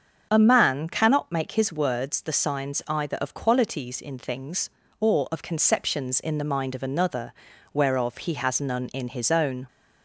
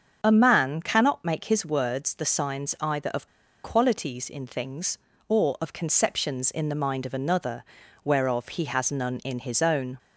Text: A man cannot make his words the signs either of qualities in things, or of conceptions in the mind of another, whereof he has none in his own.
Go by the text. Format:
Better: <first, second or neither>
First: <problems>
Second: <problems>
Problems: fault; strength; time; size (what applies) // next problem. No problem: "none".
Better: first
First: starts louder than the rest; until 1.3 s; 7 dB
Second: starts louder than the rest; until 1.2 s; 7 dB // pauses between "of" and "qualities"; at 3.2 s; 0.36 s long